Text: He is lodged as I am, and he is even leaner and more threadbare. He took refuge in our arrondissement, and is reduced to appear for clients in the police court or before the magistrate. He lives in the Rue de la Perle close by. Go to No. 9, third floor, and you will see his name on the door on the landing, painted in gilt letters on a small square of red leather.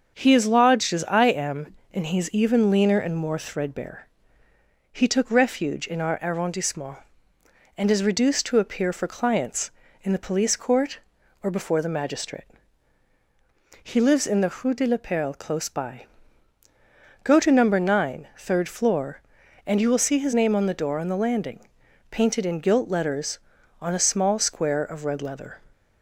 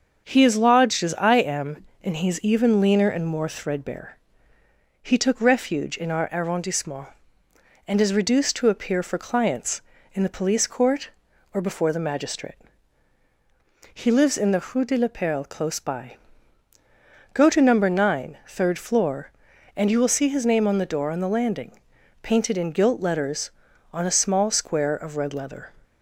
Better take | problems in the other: neither | starts louder than the rest; the same in both

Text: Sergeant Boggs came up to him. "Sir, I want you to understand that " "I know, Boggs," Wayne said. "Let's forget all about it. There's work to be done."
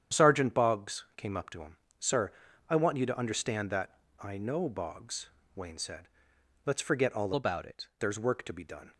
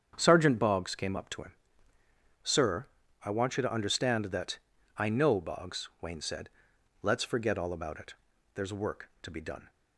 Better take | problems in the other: second | starts louder than the rest; strong; until 1.2 s; 9.5 dB; strong in the second // changes voice from "about" to "it"; from 7.3 to 7.8 s; 0.5 s long

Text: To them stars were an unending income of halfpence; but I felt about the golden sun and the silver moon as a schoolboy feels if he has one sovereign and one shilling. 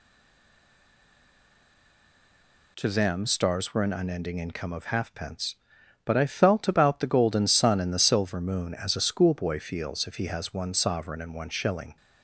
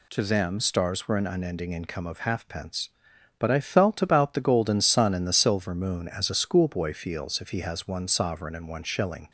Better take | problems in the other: second | stays silent before the first word; strong; until 2.7 s; 2.7 s long

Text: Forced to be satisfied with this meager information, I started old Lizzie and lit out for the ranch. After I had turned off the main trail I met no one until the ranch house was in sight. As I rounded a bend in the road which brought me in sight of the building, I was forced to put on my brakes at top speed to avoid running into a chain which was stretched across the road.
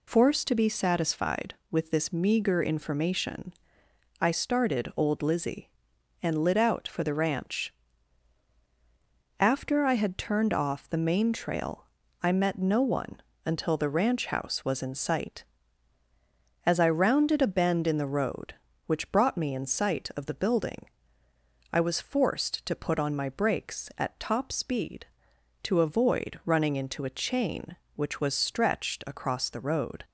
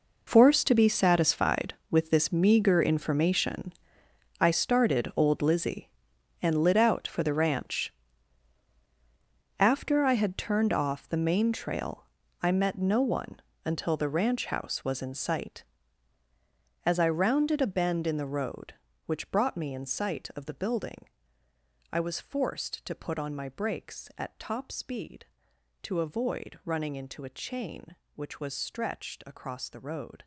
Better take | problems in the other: first | gets quieter; strong; throughout; 14.5 dB // pauses between "trail" and "I"; at 12.0 s; 0.38 s long; also in the first // pauses between "one" and "until"; slight; at 13.3 s; 0.24 s long; slight in the first

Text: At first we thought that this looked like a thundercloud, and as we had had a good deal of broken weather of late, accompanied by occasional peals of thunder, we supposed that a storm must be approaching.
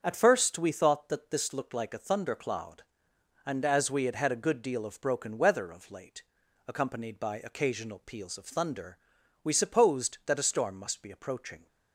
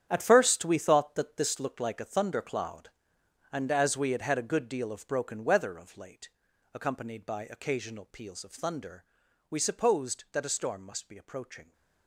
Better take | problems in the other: first | gets quieter; strong; throughout; 12 dB // starts louder than the rest; strong; until 1.1 s; 9.5 dB; also in the first

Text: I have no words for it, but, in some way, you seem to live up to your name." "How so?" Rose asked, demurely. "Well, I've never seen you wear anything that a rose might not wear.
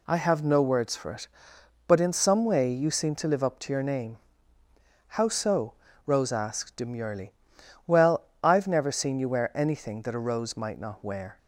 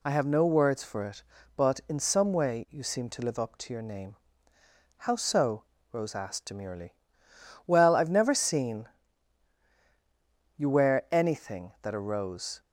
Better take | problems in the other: first | pauses between "seen" and "you"; strong; at 8.8 s; 1.7 s long // stops before "might not wear"; at 12.6 s

